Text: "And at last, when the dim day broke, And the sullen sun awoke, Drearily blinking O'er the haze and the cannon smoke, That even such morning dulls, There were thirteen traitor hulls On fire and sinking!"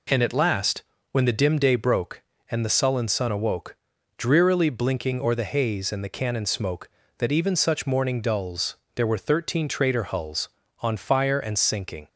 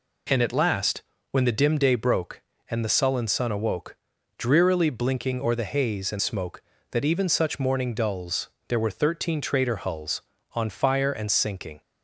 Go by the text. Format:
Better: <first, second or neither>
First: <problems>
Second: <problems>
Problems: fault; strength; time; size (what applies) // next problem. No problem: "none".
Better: first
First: none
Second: skips "the cannon"; at 6.1 s